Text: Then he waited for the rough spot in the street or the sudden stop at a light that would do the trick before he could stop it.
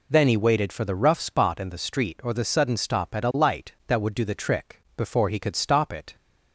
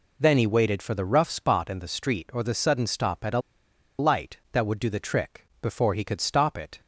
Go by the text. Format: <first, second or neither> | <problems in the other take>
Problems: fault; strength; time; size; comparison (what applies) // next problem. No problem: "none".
first | pauses between "a" and "light"; noticeable; at 3.4 s; 0.58 s long